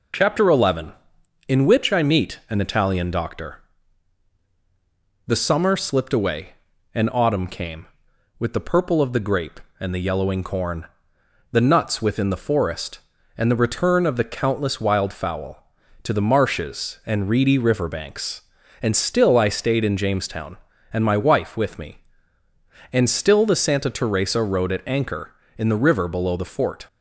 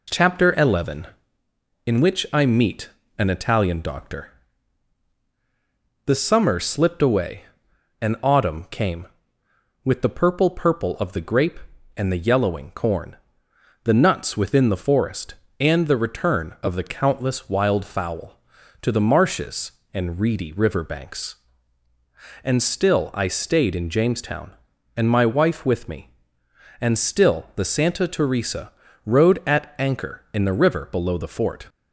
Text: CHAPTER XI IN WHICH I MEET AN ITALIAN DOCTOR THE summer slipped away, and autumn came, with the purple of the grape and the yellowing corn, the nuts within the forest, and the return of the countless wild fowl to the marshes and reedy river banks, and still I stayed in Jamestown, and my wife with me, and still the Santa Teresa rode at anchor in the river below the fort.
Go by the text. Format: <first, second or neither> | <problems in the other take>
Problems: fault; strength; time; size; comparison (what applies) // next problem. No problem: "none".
first | pauses between "MEET" and "AN"; slight; at 2.8 s; 0.30 s long // pauses between "DOCTOR" and "THE"; strong; at 4.3 s; 1.7 s long; strong in the first // says "purple" twice; at 10.4 s // pauses between "Teresa" and "rode"; slight; at 28.7 s; 0.32 s long